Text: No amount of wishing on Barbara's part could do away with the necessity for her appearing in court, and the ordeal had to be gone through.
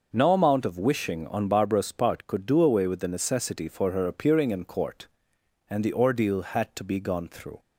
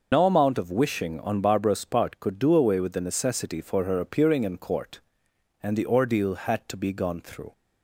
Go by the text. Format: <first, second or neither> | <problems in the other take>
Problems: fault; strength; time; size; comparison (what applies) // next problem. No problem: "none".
first | loses the start of "No"; at 0.1 s; 60 ms